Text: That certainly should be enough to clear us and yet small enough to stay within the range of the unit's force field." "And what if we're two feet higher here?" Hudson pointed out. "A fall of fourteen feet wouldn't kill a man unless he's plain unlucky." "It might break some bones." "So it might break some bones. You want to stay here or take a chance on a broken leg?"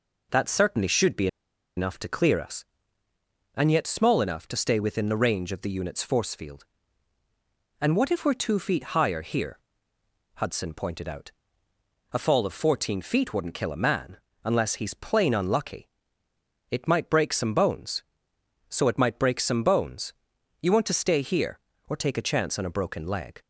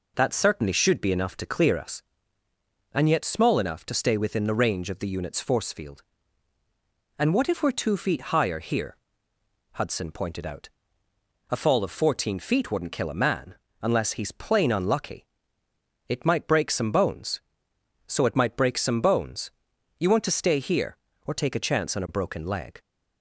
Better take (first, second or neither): second